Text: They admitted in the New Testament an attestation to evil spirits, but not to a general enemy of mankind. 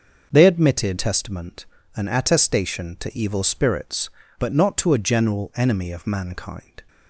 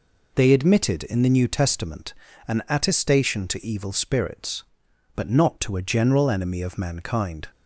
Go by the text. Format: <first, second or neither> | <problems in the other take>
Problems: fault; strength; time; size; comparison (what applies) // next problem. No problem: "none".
second | skips "in the New"; at 0.9 s // pauses between "Testament" and "an"; slight; at 1.6 s; 0.28 s long; slight in the second